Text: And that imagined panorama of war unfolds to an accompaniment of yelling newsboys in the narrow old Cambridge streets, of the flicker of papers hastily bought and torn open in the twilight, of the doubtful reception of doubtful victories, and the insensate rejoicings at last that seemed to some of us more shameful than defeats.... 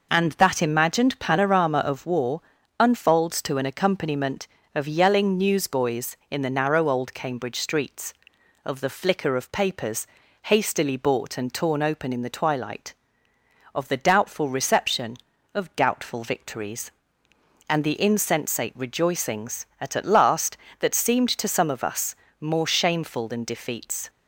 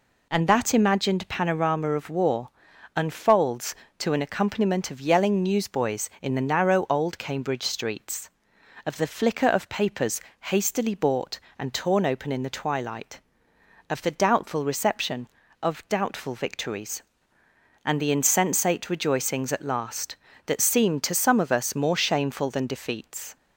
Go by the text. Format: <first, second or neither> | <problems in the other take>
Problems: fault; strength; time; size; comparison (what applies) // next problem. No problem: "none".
second | pauses between "war" and "unfolds"; at 2.4 s; 0.38 s long; noticeable in the second // pauses between "papers" and "hastily"; slight; at 10.0 s; 0.36 s long; slight in the second // says "at" twice; at 19.9 s // pauses between "us" and "more"; slight; at 22.1 s; 0.26 s long